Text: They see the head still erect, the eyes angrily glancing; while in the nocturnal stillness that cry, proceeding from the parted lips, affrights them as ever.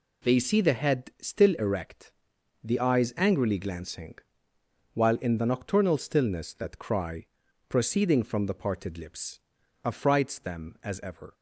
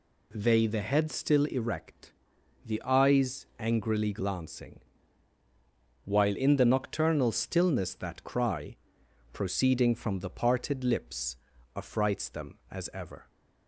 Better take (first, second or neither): first